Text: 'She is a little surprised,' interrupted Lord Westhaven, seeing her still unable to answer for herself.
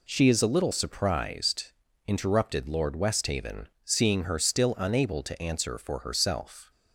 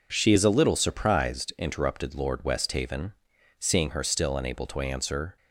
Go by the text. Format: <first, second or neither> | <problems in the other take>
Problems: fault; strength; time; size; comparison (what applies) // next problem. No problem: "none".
first | stops before "for herself"; at 5.3 s